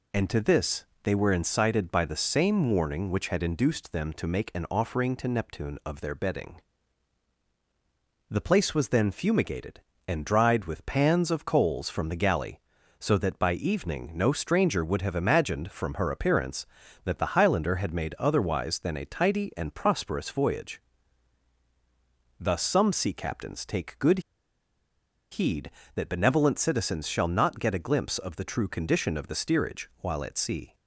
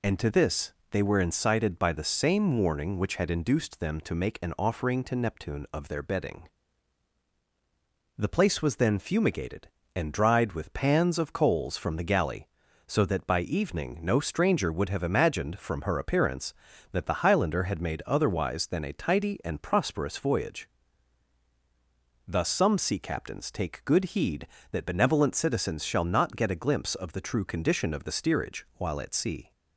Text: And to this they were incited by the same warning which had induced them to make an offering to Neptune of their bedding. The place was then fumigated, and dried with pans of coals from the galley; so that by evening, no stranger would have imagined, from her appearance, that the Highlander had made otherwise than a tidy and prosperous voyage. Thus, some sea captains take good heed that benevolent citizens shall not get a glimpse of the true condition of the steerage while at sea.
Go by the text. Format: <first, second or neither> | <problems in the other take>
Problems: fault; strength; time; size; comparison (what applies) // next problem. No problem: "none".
second | pauses between "this" and "they"; slight; at 0.8 s; 0.18 s long; slight in the second // pauses between "good" and "heed"; at 24.1 s; 1.1 s long